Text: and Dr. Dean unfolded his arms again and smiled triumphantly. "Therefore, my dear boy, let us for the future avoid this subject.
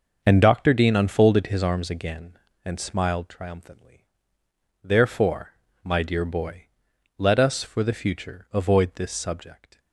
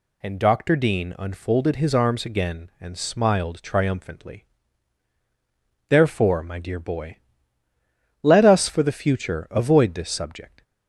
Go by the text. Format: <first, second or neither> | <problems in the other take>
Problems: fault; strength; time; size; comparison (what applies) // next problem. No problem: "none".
second | gets quieter; strong; throughout; 9.5 dB